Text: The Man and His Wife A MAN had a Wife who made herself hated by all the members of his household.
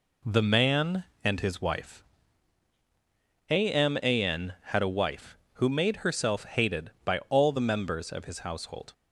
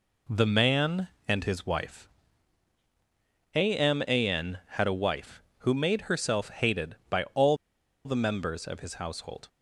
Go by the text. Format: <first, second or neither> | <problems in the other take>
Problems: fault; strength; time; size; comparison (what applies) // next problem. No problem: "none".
first | pauses between "Wife" and "A"; strong; at 2.0 s; 1.4 s long; strong in the first // pauses between "all" and "the"; noticeable; at 7.5 s; 0.49 s long